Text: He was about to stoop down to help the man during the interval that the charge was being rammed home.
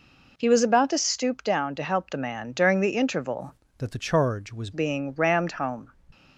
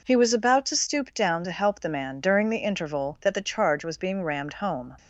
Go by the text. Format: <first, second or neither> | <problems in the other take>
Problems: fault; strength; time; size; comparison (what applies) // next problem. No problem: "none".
second | changes voice from "that" to "was"; from 3.7 to 4.6 s; 0.9 s long